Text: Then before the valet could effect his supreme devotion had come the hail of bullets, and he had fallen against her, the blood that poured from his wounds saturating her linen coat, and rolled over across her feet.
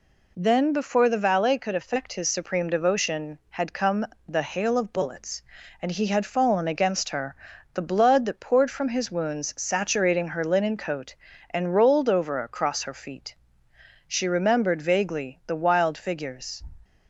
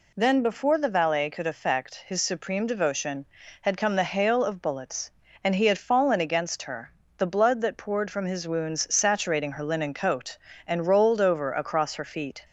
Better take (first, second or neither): second